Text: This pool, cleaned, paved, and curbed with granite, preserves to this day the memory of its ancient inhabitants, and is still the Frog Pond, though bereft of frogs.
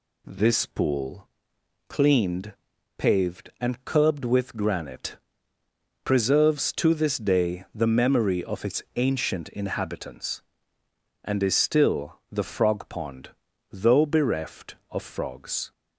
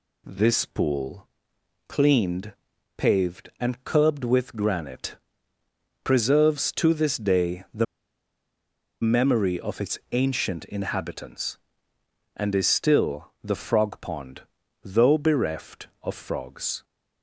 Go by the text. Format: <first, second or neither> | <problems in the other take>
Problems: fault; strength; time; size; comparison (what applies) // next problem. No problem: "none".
first | pauses between "the" and "memory"; at 7.8 s; 1.1 s long